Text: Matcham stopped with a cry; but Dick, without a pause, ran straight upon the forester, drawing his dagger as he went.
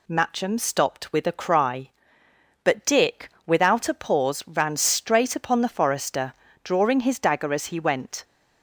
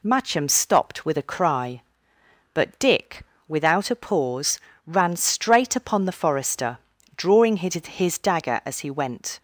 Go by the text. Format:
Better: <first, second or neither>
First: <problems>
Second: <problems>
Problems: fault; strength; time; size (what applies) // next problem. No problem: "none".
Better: first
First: none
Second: says "his" twice; at 7.7 s